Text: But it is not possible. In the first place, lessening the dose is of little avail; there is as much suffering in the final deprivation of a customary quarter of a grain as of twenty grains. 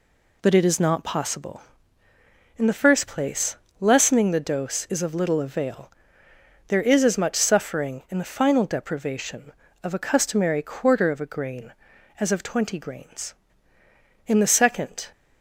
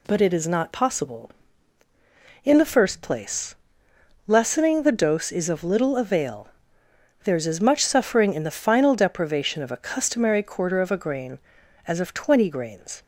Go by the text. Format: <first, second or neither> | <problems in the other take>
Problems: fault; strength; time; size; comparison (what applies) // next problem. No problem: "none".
second | goes on to say "In the second"; noticeable; from 14.2 s on; 0.84 s long